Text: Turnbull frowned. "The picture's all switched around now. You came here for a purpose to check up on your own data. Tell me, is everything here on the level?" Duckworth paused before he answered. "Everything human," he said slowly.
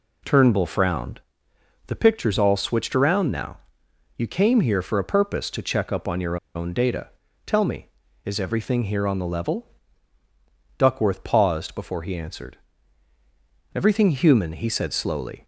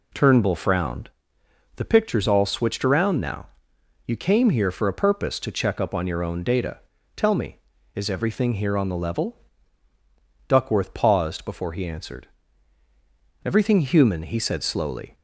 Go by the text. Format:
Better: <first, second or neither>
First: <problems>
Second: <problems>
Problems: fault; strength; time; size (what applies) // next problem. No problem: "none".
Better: second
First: pauses between "your" and "own"; slight; at 6.3 s; 0.19 s long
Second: none